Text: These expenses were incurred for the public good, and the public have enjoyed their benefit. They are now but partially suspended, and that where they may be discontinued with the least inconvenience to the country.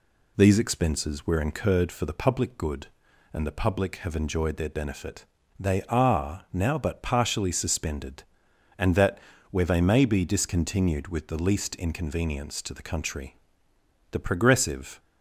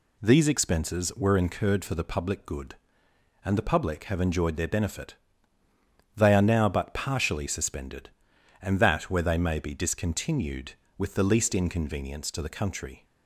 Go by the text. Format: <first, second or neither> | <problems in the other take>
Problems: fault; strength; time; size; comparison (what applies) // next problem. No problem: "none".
second | pauses between "that" and "where"; slight; at 9.1 s; 0.32 s long // goes on to say "The progressive"; noticeable; from 14.1 s on; 0.88 s long